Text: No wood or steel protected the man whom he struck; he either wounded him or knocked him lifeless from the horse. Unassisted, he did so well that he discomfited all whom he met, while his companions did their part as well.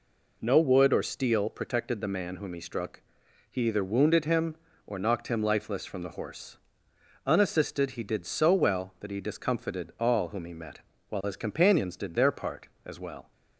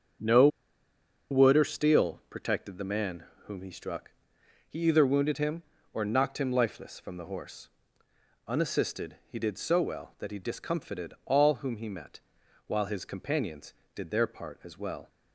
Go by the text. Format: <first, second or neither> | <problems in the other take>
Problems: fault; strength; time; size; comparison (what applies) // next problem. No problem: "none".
first | starts louder than the rest; strong; until 2.0 s; 7.5 dB // pauses between "No" and "wood"; noticeable; at 0.4 s; 0.82 s long // pauses between "man" and "whom"; slight; at 3.2 s; 0.22 s long